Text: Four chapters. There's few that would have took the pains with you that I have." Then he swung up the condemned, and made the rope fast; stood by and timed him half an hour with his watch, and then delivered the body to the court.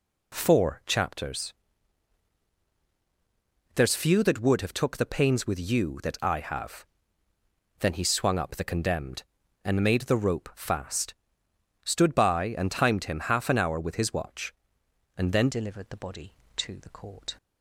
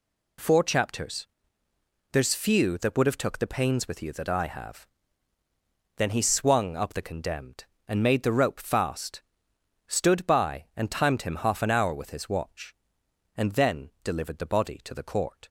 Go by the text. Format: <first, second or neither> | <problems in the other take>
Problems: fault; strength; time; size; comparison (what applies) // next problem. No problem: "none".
second | changes voice at "delivered"; from 15.4 s on; 1.9 s long